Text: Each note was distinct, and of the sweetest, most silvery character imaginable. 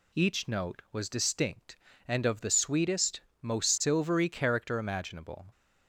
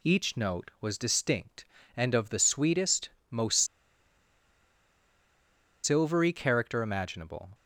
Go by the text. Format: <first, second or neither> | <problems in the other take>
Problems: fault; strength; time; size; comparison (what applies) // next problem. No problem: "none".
first | pauses between "most" and "silvery"; strong; at 3.5 s; 2.2 s long